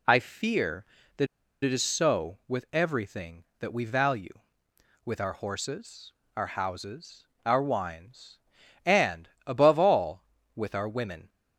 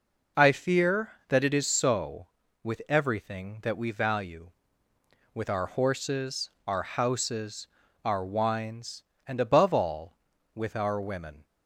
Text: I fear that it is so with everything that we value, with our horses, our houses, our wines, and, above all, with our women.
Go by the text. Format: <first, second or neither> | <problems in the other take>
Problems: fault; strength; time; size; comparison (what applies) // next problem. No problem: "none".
second | pauses between "that" and "it"; at 1.2 s; 0.38 s long